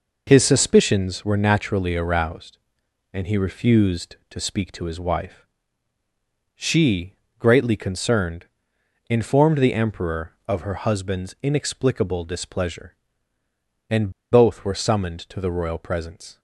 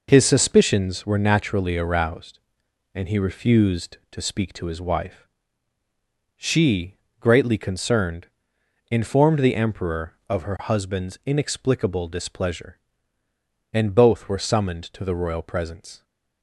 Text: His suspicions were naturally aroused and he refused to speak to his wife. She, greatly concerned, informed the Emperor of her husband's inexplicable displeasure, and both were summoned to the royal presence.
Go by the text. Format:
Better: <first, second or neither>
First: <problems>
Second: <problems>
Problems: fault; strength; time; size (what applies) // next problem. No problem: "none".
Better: second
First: pauses between "and" and "both"; slight; at 14.1 s; 0.19 s long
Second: none